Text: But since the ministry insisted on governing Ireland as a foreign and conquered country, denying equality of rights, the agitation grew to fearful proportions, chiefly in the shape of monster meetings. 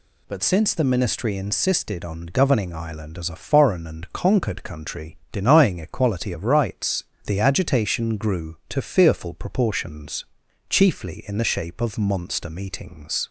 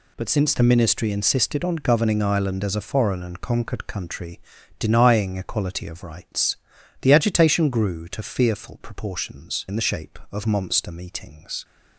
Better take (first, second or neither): first